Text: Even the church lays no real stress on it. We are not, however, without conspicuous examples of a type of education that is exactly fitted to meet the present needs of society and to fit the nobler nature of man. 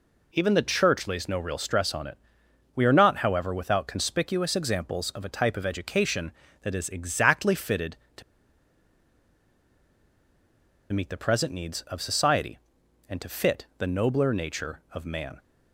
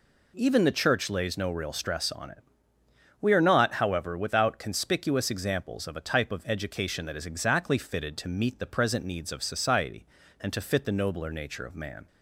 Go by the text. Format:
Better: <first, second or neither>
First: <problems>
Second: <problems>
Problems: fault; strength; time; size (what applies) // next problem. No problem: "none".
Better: second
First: pauses between "to" and "meet"; strong; at 8.2 s; 2.7 s long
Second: none